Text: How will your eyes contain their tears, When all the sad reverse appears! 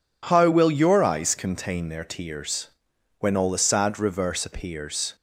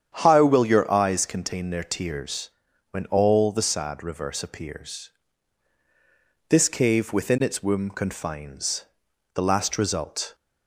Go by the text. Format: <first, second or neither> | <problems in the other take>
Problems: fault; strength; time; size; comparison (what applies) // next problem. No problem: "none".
first | starts louder than the rest; strong; until 1.2 s; 8.5 dB // goes on to say "This cave within its womb confines The last result"; strong; from 6.4 s on; 3.8 s long